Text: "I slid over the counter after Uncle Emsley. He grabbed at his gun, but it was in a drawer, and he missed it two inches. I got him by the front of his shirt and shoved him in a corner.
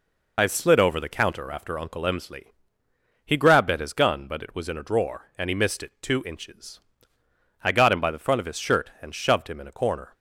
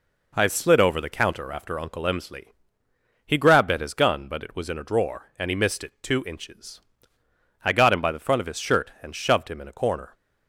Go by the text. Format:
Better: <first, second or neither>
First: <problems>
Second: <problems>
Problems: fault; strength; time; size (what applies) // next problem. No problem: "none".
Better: second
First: loses the start of "I"; at 0.3 s; 50 ms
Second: none